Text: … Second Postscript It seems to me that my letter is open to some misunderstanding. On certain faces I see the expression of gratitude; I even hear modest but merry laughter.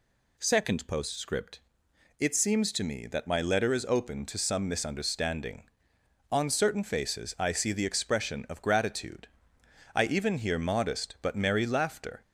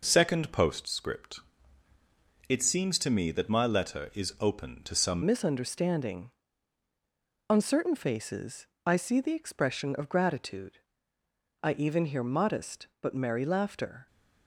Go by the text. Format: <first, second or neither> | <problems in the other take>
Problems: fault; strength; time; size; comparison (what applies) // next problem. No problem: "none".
first | pauses between "Postscript" and "It"; at 1.3 s; 1.1 s long; noticeable in the first // changes voice at "misunderstanding"; from 5.2 s on; 8.8 s long // pauses between "faces" and "I"; slight; at 8.6 s; 0.18 s long